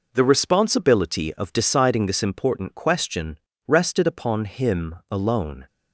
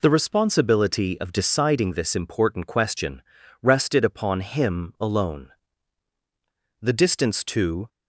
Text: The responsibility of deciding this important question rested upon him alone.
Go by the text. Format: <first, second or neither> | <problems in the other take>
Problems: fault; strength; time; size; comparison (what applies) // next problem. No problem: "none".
first | pauses between "question" and "rested"; at 3.2 s; 0.40 s long; slight in the first // goes on to say "The distance to"; noticeable; from 6.8 s on; 1.0 s long